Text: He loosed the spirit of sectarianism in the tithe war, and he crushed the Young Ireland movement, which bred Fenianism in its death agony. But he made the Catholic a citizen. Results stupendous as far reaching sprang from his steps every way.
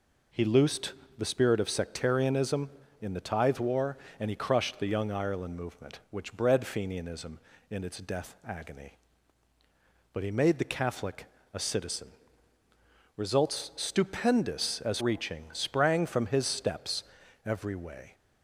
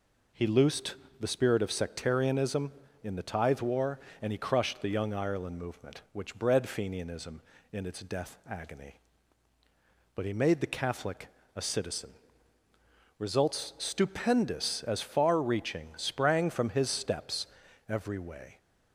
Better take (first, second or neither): second